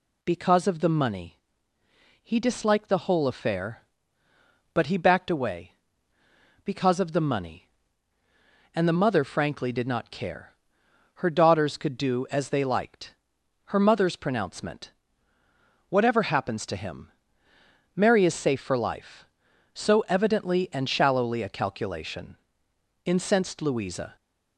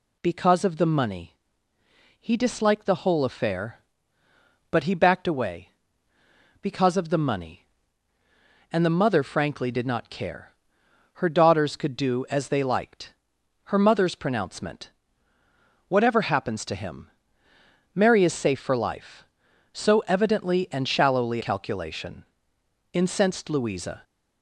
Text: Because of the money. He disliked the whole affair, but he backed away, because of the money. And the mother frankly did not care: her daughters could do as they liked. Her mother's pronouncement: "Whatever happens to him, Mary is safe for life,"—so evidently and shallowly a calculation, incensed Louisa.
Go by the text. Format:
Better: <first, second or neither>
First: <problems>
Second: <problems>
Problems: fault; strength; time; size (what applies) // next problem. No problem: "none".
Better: first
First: none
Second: skips "a"; at 21.4 s